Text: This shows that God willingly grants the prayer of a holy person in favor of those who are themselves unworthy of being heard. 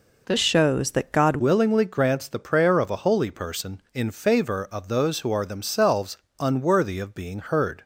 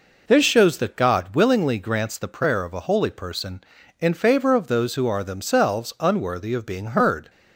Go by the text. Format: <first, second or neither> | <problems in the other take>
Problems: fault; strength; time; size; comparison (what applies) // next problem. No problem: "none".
second | changes voice from "shows" to "God"; from 0.3 to 1.3 s; 1.0 s long // pauses between "themselves" and "unworthy"; slight; at 6.1 s; 0.20 s long